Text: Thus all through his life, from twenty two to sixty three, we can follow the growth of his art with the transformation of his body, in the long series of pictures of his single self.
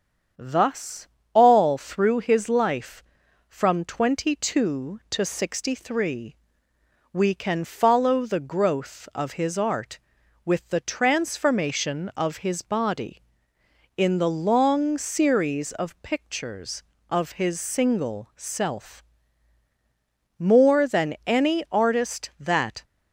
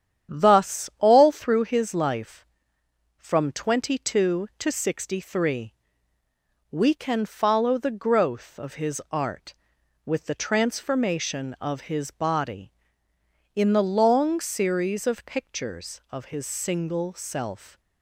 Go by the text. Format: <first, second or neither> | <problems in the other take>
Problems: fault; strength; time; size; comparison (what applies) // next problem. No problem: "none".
second | starts louder than the rest; strong; until 1.6 s; 8 dB; strong in the second // pauses between "Thus" and "all"; slight; at 1.0 s; 0.26 s long // goes on to say "More than any artist that"; strong; from 20.3 s on; 2.4 s long